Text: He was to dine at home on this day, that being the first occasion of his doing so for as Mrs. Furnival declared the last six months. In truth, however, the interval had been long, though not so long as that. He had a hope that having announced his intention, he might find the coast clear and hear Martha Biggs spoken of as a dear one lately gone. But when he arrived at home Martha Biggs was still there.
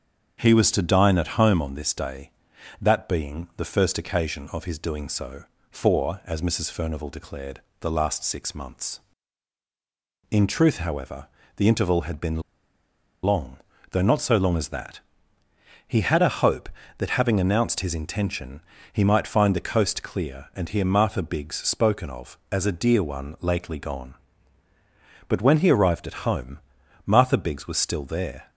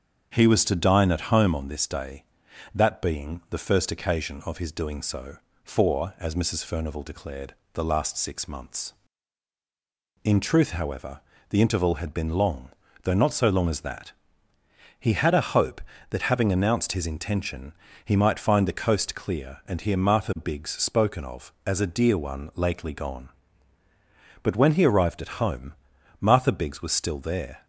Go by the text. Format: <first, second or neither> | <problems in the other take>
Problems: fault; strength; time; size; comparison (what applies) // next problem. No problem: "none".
second | starts louder than the rest; strong; until 1.4 s; 7 dB; strong in the second // pauses between "declared" and "the"; slight; at 7.5 s; 0.22 s long; slight in the second // pauses between "been" and "long"; noticeable; at 12.4 s; 0.84 s long // pauses between "home" and "Martha"; at 26.6 s; 0.44 s long; also in the second